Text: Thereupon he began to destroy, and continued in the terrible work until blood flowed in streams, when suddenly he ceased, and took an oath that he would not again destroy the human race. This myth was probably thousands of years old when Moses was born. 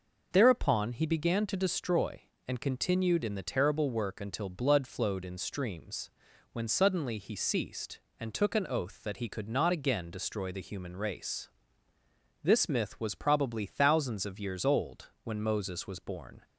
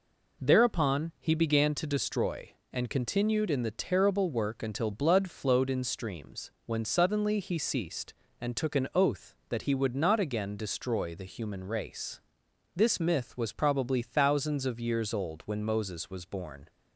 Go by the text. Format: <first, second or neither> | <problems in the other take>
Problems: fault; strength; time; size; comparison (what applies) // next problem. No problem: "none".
second | says "could" for "would"; at 9.2 s